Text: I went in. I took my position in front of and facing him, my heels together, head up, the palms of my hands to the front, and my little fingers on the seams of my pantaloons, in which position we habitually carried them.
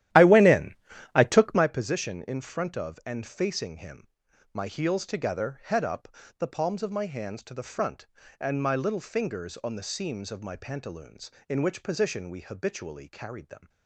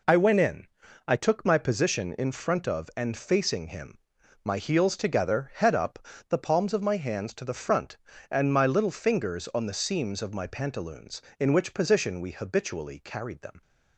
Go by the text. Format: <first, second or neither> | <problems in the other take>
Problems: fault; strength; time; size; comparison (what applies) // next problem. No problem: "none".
second | starts louder than the rest; strong; until 1.7 s; 13 dB